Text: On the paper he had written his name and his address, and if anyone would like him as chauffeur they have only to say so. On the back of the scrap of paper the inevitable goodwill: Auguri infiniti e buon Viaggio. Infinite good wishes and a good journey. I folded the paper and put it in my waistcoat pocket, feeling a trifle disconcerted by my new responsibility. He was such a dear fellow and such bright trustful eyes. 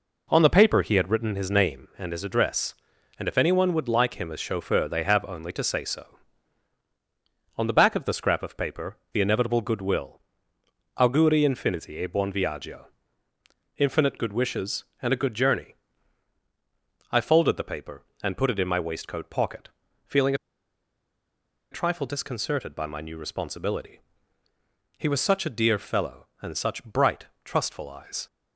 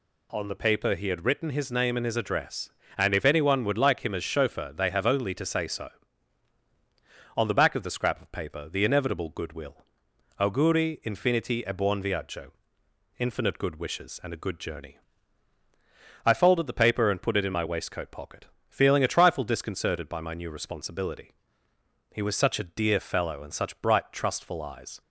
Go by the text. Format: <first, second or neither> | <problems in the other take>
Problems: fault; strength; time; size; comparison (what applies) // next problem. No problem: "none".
second | pauses between "paper" and "the"; slight; at 8.9 s; 0.18 s long // pauses between "feeling" and "a"; strong; at 20.3 s; 1.3 s long // pauses between "bright" and "trustful"; slight; at 27.2 s; 0.18 s long